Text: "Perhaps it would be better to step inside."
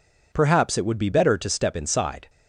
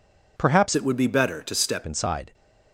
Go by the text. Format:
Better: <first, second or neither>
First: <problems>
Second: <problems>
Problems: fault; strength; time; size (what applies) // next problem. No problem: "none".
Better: first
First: none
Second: changes voice from "it" to "step"; from 0.7 to 1.8 s; 1.1 s long